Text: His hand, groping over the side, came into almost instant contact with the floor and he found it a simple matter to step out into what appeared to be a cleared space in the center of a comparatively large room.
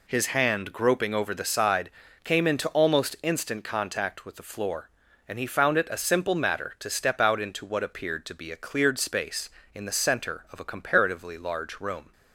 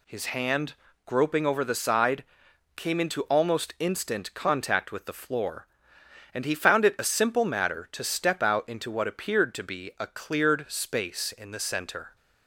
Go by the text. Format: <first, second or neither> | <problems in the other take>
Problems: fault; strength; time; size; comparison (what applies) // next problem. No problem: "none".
first | stops before "of a comparatively large room"; at 12.1 s